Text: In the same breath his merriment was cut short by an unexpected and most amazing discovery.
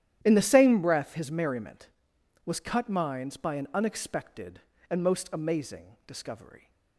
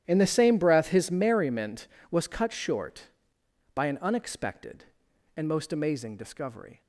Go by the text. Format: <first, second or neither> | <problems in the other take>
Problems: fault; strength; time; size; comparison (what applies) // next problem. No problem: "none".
second | starts louder than the rest; strong; until 1.2 s; 11.5 dB; strong in the second // says "minds" for "short"; at 2.8 s